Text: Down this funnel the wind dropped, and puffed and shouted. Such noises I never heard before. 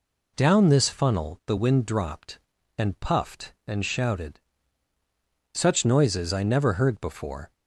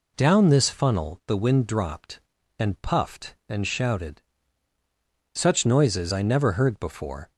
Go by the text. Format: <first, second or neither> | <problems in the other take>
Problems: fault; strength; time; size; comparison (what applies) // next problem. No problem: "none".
neither | none